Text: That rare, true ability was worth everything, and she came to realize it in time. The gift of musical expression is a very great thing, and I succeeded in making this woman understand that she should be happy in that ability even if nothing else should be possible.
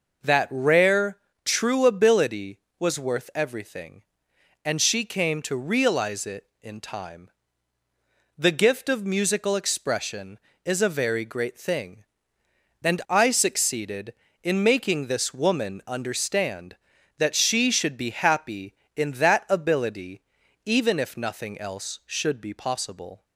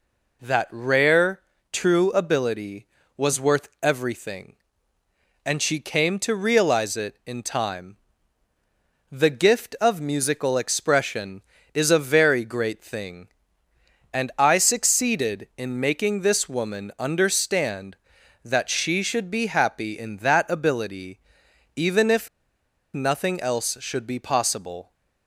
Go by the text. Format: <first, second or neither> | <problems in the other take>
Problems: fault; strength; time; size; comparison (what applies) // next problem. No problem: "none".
first | pauses between "ability" and "even"; noticeable; at 21.1 s; 0.58 s long; also in the first // pauses between "if" and "nothing"; noticeable; at 22.2 s; 0.66 s long